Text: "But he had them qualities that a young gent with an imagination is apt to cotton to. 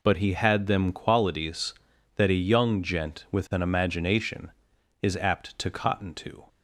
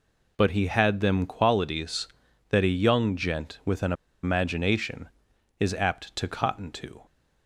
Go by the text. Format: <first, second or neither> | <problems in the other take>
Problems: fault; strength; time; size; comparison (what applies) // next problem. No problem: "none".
first | pauses between "an" and "imagination"; slight; at 3.9 s; 0.30 s long